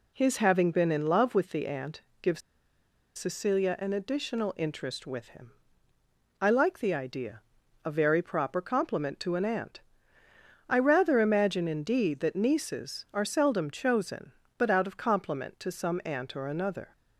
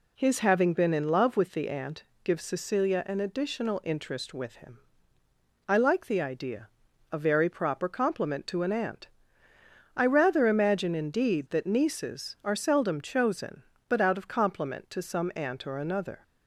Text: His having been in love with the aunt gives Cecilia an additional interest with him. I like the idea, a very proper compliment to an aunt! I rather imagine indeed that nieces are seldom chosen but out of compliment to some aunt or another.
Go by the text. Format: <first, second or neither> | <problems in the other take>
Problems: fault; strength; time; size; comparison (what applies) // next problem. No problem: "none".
second | pauses between "aunt" and "gives"; slight; at 2.0 s; 0.18 s long; slight in the second // pauses between "gives" and "Cecilia"; noticeable; at 2.4 s; 0.77 s long